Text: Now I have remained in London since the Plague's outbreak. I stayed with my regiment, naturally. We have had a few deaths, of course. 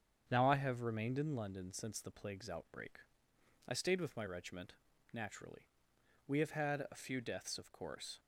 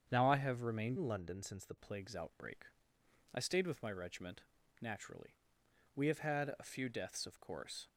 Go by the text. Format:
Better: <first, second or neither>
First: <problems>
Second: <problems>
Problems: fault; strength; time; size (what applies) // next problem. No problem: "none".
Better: first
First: starts louder than the rest; strong; until 1.3 s; 7.5 dB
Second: starts louder than the rest; strong; until 1.1 s; 7.5 dB // changes voice from "in" to "the"; from 0.9 to 1.7 s; 0.8 s long